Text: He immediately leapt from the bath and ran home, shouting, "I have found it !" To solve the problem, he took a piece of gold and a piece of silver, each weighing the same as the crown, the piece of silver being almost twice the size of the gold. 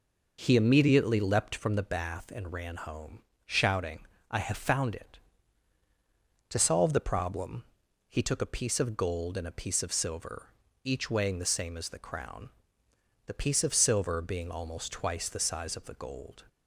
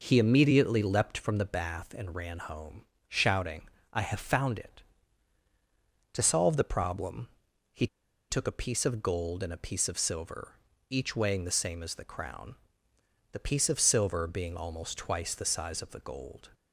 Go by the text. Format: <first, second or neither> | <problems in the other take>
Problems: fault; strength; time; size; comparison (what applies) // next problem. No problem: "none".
first | pauses between "he" and "took"; at 7.8 s; 0.44 s long